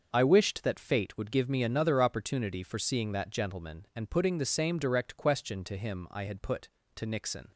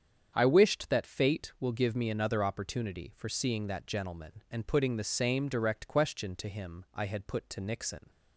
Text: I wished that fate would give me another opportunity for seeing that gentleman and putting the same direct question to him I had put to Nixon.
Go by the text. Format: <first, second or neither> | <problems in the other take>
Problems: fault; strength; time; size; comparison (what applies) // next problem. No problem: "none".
first | starts louder than the rest; strong; until 1.3 s; 8 dB; also in the first // says "will" for "would"; at 1.5 s